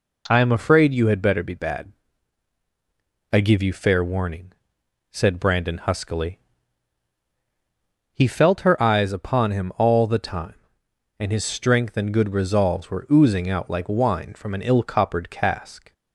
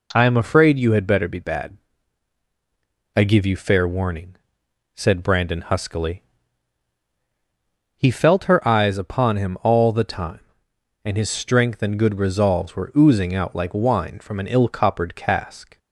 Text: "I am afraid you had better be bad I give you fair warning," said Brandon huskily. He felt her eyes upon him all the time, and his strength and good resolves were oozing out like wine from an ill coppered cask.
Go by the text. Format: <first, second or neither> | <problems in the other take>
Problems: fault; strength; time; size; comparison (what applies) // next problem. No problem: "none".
neither | pauses between "bad" and "I"; strong; the same in both